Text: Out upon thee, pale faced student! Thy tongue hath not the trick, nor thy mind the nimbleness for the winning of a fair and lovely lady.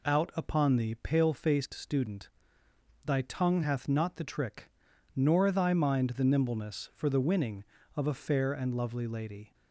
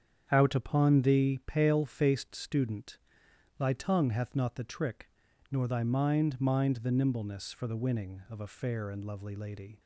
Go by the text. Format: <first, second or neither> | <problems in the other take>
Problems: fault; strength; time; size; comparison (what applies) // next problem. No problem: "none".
first | starts louder than the rest; strong; until 1.3 s; 8.5 dB // says "mind" twice; at 6.4 s